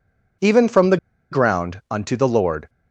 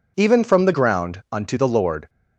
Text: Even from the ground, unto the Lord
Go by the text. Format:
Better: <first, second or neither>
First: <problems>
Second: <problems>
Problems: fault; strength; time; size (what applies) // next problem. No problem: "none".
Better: second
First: pauses between "the" and "ground"; slight; at 0.9 s; 0.34 s long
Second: none